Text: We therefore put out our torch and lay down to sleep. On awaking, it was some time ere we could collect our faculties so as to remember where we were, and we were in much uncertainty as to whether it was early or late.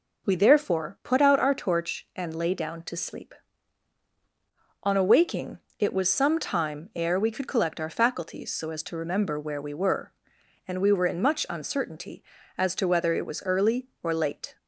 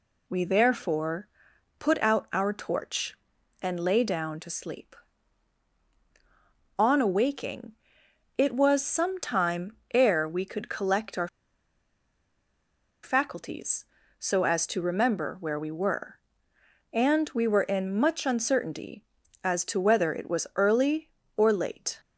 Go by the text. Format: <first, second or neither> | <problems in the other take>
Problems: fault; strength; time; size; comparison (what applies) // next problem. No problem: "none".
first | pauses between "therefore" and "put"; noticeable; at 1.2 s; 0.50 s long // pauses between "time" and "ere"; slight; at 9.7 s; 0.18 s long // pauses between "our" and "faculties"; strong; at 11.2 s; 1.7 s long